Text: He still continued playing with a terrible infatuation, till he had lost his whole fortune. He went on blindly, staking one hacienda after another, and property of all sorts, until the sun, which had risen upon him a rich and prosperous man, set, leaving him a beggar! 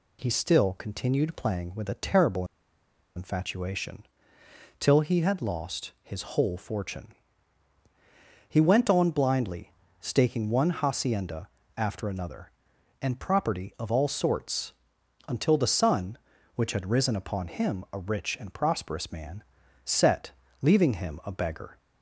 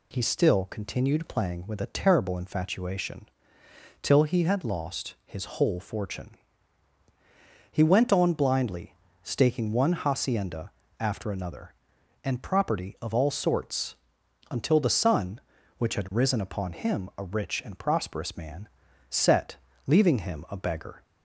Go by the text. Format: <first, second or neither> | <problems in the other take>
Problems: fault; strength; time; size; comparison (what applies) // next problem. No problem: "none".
second | pauses between "terrible" and "infatuation"; noticeable; at 2.4 s; 0.71 s long // pauses between "hacienda" and "after"; slight; at 11.4 s; 0.30 s long; slight in the second